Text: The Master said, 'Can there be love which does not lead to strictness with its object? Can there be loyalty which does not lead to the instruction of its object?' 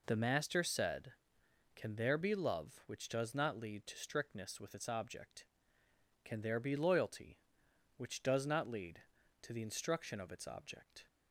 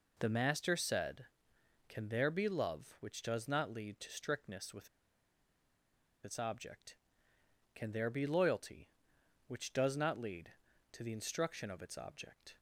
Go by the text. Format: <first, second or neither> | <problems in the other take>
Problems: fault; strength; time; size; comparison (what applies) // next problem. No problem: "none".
first | pauses between "with" and "its"; strong; at 4.8 s; 1.3 s long